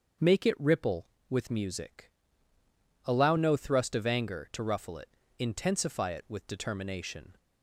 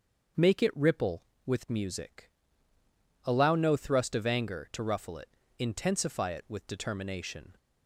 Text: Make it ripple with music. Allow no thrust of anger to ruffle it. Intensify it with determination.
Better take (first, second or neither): neither